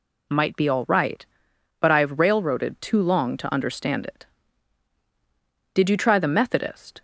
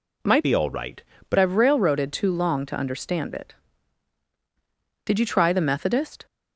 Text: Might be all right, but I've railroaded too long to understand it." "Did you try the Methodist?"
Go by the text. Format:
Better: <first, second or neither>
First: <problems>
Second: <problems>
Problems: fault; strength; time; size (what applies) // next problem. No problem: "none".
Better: first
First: none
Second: changes voice from "be" to "but"; from 0.4 to 1.3 s; 0.9 s long